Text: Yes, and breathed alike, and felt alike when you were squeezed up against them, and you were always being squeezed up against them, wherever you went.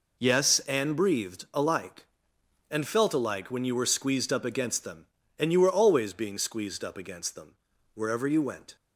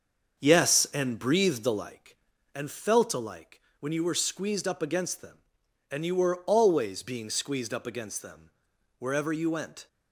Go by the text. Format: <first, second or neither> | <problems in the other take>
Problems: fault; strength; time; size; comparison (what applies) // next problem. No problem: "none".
first | starts louder than the rest; until 2.1 s; 7 dB // pauses between "alike" and "when"; slight; at 3.5 s; 0.20 s long